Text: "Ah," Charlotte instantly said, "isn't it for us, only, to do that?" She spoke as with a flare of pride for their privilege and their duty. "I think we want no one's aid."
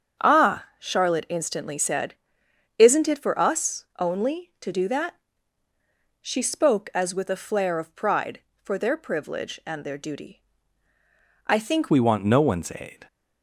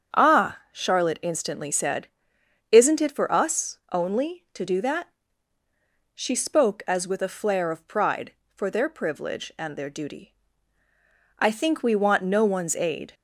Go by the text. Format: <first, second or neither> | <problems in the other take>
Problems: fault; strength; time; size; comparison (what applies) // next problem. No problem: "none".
second | starts louder than the rest; strong; until 1.3 s; 7 dB; strong in the second // changes voice at "we"; from 11.8 s on; 1.2 s long